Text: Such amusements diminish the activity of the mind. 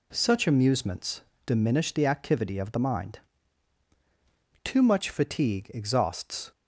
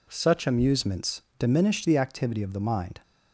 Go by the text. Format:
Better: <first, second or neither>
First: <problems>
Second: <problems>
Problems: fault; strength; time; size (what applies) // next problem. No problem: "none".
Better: second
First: pauses between "amusements" and "diminish"; slight; at 1.2 s; 0.24 s long // goes on to say "Too much fatigue exhausts"; strong; from 4.6 s on; 1.8 s long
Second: pauses between "amusements" and "diminish"; slight; at 1.2 s; 0.18 s long